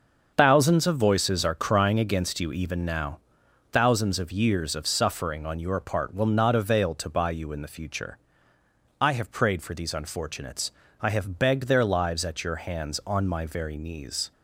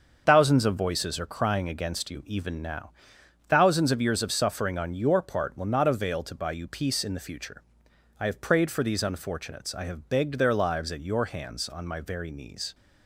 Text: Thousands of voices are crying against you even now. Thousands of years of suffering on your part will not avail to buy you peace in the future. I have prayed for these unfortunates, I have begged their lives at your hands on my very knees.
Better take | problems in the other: second | starts louder than the rest; until 1.3 s; 6.5 dB; also in the second // skips "peace"; at 7.5 s

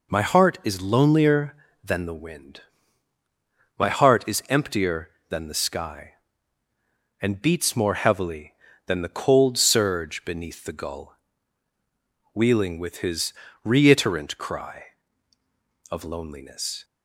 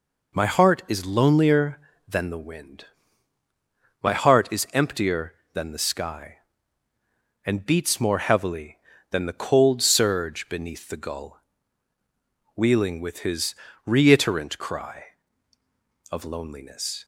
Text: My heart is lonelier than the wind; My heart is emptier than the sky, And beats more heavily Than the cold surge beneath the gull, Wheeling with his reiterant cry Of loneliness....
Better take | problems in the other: neither | pauses between "his" and "reiterant"; slight; the same in both

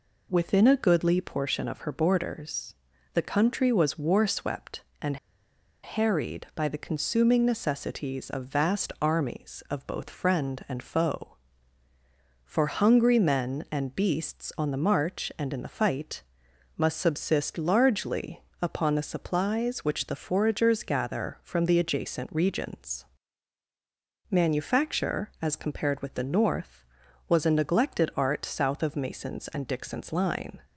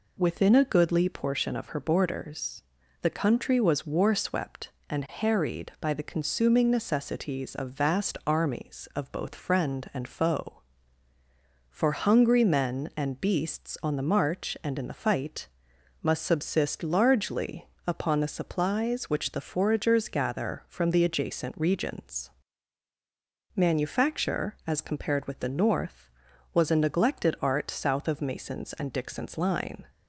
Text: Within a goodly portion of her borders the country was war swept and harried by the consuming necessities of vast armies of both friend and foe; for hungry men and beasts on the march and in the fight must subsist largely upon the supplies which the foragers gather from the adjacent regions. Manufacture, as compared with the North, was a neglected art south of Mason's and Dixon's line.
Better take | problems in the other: second | pauses between "borders" and "the"; at 2.7 s; 0.38 s long; also in the second // pauses between "and" and "harried"; noticeable; at 5.1 s; 0.67 s long // pauses between "fight" and "must"; noticeable; at 16.2 s; 0.54 s long; noticeable in the second // pauses between "largely" and "upon"; slight; at 18.4 s; 0.20 s long; slight in the second

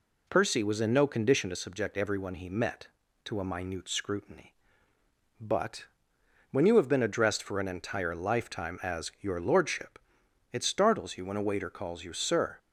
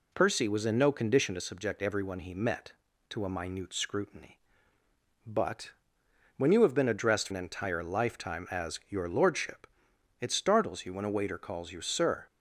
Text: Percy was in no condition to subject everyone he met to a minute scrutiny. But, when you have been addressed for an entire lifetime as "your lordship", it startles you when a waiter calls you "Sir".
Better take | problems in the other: first | skips "for"; at 7.2 s

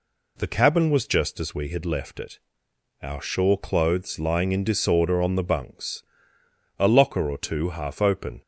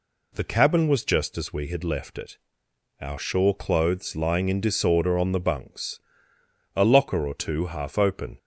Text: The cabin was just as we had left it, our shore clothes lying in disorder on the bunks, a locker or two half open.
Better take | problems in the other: neither | none

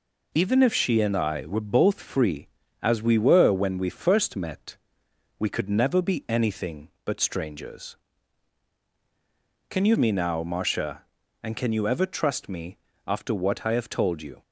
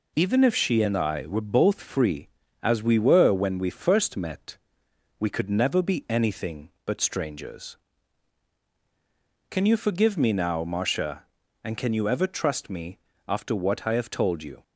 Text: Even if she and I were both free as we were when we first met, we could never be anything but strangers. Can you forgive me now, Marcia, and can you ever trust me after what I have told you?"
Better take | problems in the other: second | skips "forgive"; at 9.9 s // pauses between "me" and "after"; slight; at 12.7 s; 0.28 s long; slight in the second

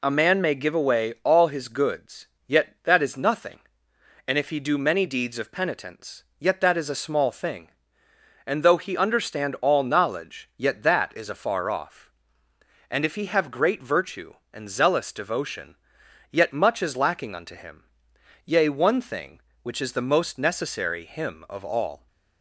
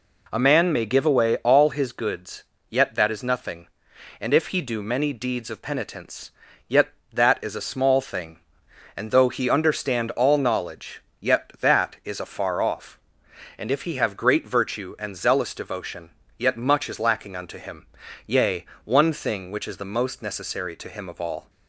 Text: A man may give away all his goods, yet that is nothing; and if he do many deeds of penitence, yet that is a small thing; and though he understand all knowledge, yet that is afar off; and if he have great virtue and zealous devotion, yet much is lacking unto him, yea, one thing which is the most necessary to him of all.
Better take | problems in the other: second | skips "to"; at 21.0 s

